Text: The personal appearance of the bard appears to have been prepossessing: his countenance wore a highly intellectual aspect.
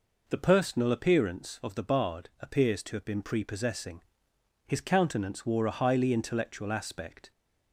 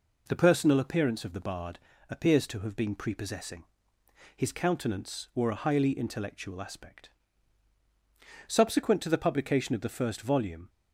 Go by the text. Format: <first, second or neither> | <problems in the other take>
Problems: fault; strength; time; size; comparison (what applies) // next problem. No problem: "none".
first | pauses between "bard" and "appears"; slight; at 1.7 s; 0.30 s long // goes on to say "Subsequent to the publication of the first volume"; strong; from 8.4 s on; 2.2 s long